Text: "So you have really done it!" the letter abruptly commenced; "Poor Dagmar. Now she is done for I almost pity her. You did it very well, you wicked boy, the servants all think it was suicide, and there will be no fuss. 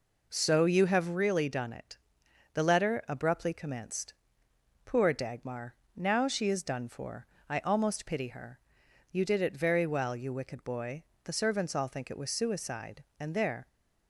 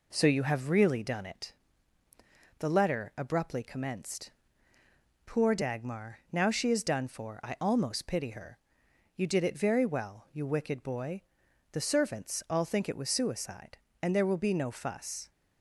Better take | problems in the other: second | pauses between "for" and "I"; slight; at 7.2 s; 0.22 s long // stops before "will be no fuss"; at 13.6 s

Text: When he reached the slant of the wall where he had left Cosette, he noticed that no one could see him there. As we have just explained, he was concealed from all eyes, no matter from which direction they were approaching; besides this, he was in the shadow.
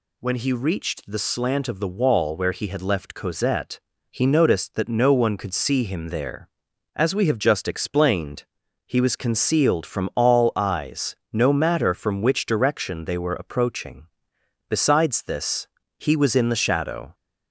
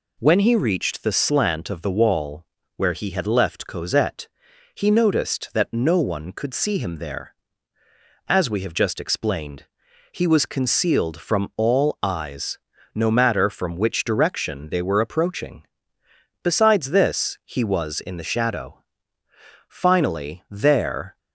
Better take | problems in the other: first | pauses between "wall" and "where"; slight; at 2.4 s; 0.32 s long // goes on to say "Finally there"; from 19.6 s on; 1.5 s long

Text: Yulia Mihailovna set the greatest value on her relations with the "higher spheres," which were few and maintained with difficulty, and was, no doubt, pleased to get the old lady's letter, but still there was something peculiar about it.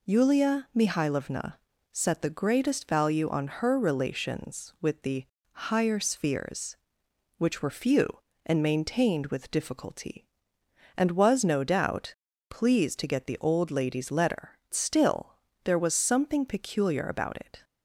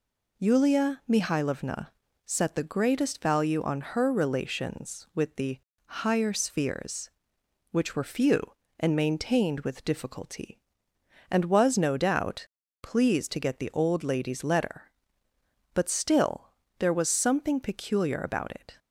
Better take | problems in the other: second | pauses between "Mihailovna" and "set"; at 1.5 s; 0.38 s long; also in the second // pauses between "the" and "higher"; slight; at 5.2 s; 0.26 s long; slight in the second // skips "but"; at 14.6 s // pauses between "still" and "there"; slight; at 15.3 s; 0.26 s long; slight in the second

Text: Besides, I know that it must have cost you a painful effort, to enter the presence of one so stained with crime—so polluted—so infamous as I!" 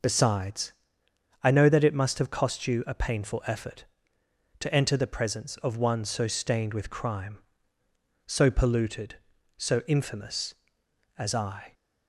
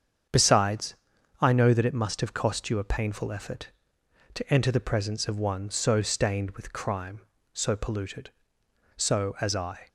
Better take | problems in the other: first | starts louder than the rest; strong; until 1.7 s; 7.5 dB // skips "infamous"; at 9.3 s

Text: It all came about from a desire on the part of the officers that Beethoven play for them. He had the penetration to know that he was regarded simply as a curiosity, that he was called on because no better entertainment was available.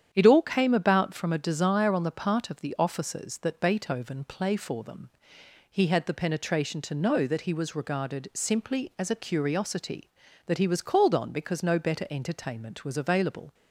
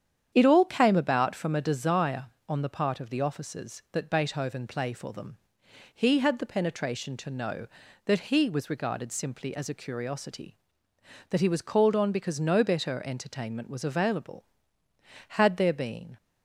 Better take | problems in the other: first | starts louder than the rest; strong; until 1.3 s; 8.5 dB; strong in the first // goes on to say "Had there been"; noticeable; from 15.2 s on; 0.88 s long

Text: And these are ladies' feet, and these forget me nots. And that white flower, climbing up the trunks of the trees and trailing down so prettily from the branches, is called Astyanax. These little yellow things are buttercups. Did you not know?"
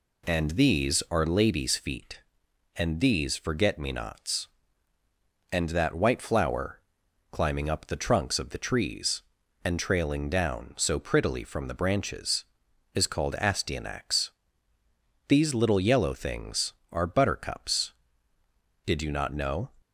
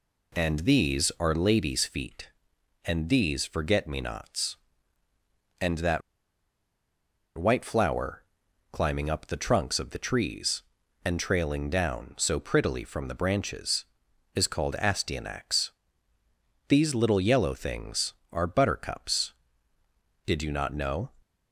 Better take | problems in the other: first | pauses between "that" and "white"; strong; at 6.0 s; 1.3 s long

